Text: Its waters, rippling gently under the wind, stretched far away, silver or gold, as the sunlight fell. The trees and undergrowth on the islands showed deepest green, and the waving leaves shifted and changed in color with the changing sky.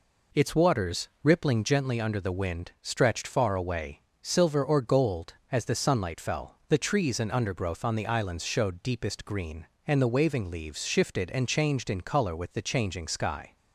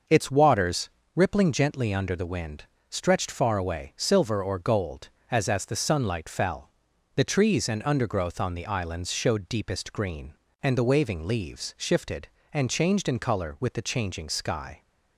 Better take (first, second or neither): first